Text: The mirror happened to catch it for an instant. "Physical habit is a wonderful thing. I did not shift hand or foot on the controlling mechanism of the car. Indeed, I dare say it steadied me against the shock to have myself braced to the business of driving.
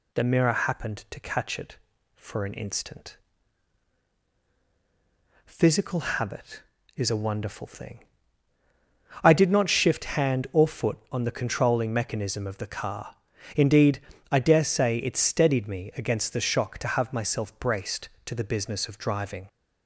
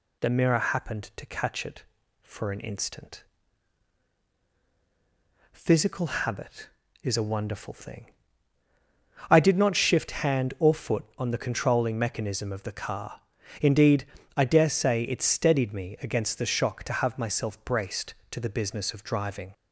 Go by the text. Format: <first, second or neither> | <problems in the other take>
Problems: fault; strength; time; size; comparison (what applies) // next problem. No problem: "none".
neither | none